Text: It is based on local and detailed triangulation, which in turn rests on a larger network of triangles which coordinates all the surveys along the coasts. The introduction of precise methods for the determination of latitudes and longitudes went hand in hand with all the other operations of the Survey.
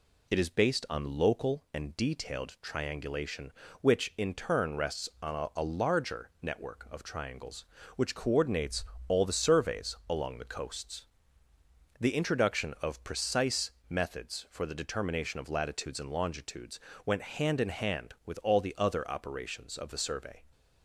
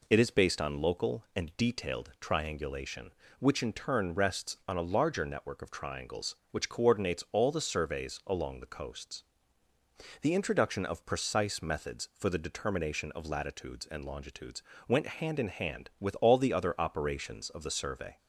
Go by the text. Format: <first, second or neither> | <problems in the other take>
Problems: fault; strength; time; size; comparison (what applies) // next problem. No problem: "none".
second | says "a" twice; at 5.5 s // pauses between "coordinates" and "all"; slight; at 8.8 s; 0.24 s long // pauses between "precise" and "methods"; slight; at 13.7 s; 0.18 s long // pauses between "longitudes" and "went"; slight; at 16.7 s; 0.28 s long; slight in the second